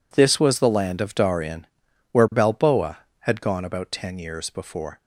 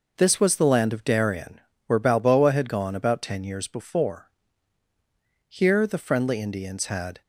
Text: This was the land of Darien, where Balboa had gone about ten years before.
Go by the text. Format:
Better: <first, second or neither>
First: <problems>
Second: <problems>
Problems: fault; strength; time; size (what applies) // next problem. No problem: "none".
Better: first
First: none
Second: goes on to say "Here the friendly Indians had"; strong; from 5.4 s on; 1.7 s long